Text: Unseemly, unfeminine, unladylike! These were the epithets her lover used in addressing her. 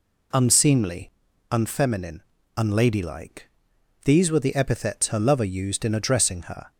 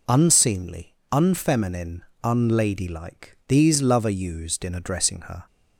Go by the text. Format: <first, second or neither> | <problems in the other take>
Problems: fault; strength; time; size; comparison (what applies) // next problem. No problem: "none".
first | skips "were the epithets her"; at 3.8 s